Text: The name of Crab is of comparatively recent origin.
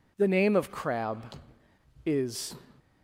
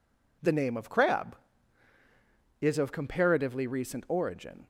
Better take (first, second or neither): second